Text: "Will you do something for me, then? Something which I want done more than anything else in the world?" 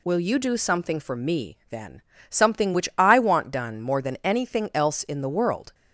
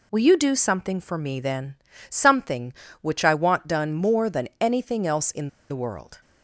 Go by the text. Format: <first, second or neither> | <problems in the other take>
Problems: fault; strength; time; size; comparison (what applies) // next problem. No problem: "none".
first | pauses between "in" and "the"; slight; at 5.4 s; 0.21 s long